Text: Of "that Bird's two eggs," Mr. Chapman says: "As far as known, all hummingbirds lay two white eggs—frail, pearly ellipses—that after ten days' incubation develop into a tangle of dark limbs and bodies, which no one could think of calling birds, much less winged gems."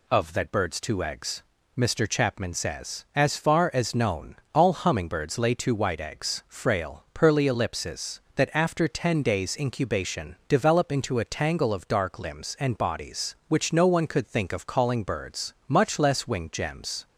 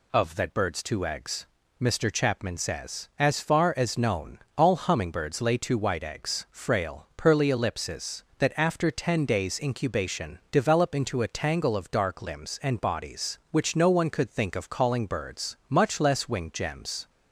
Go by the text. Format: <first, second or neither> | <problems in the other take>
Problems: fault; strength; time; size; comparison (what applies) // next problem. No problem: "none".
neither | none